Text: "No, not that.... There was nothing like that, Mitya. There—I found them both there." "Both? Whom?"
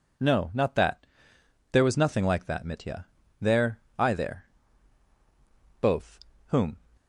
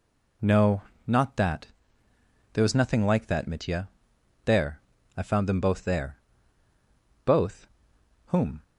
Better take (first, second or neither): second